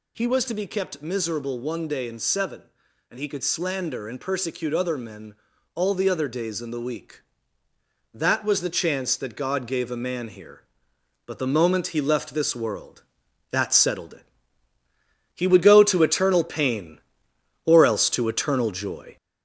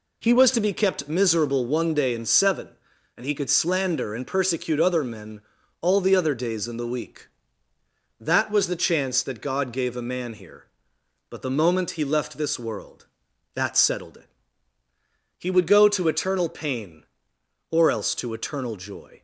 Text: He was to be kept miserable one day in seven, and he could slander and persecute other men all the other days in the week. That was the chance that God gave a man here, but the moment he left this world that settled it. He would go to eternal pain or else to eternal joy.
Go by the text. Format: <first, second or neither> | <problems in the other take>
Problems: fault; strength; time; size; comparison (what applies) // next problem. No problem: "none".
second | gets louder; throughout; 4 dB // pauses between "men" and "all"; at 5.3 s; 0.40 s long; also in the second